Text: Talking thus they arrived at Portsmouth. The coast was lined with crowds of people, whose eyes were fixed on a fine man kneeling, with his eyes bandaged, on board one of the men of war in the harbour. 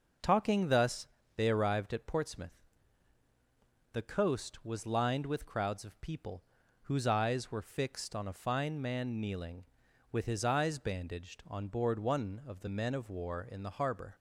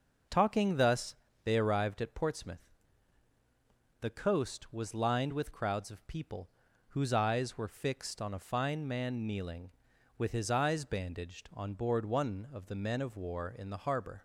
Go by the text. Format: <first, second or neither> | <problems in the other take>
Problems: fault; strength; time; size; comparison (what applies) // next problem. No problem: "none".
neither | pauses between "thus" and "they"; slight; the same in both